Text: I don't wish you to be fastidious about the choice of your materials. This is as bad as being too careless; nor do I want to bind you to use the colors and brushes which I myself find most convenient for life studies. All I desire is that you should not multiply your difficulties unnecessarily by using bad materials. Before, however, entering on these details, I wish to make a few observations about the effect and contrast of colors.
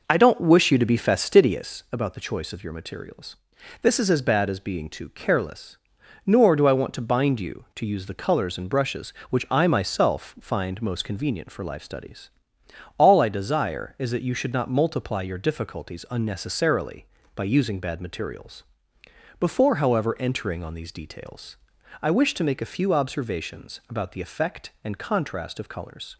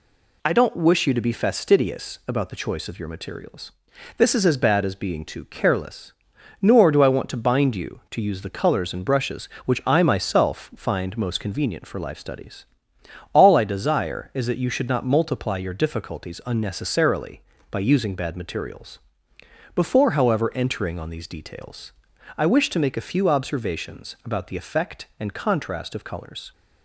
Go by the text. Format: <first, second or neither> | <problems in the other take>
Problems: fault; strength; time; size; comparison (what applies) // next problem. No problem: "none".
second | starts louder than the rest; noticeable; until 1.7 s; 5 dB